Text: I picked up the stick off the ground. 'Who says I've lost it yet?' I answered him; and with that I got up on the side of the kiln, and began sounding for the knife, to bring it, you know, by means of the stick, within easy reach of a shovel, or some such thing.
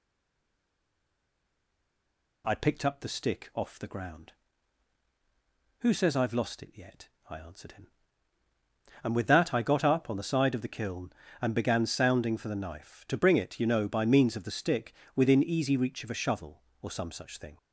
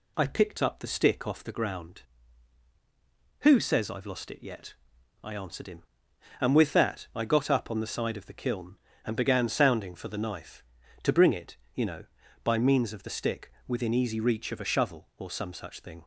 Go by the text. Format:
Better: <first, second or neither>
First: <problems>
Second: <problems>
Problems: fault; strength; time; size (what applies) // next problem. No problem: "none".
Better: second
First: stays silent before the first word; until 2.4 s; 2.4 s long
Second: none